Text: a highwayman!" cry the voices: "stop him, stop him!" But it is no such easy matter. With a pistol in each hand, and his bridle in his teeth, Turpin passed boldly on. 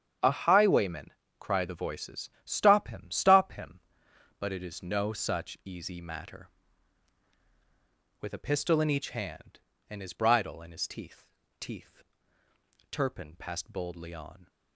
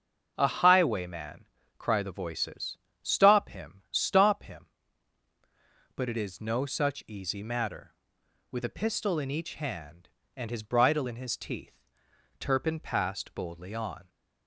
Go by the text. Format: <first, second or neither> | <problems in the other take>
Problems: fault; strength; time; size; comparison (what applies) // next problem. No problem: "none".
second | starts louder than the rest; strong; until 1.5 s; 8 dB; also in the second // says "teeth" twice; at 11.6 s